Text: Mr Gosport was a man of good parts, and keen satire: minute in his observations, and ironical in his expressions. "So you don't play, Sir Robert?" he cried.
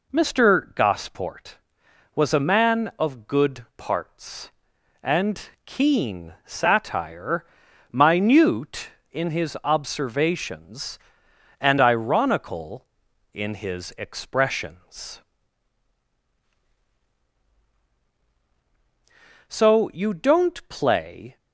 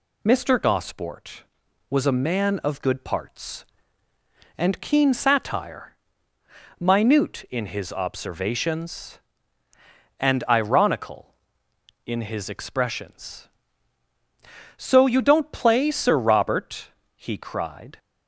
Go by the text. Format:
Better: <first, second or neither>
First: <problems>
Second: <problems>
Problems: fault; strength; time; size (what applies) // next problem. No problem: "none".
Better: second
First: pauses between "and" and "keen"; slight; at 5.5 s; 0.16 s long // stops before "Sir Robert he cried"; at 21.3 s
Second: none